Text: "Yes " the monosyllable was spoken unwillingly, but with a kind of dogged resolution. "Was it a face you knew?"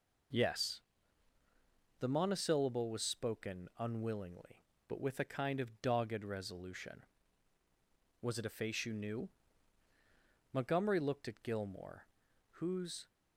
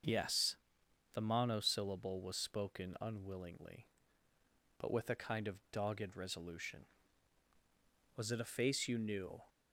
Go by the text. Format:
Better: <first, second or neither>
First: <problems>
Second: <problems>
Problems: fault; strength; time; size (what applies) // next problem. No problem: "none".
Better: second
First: goes on to say "Montgomery looked at Gilmore whose"; strong; from 10.5 s on; 2.5 s long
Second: none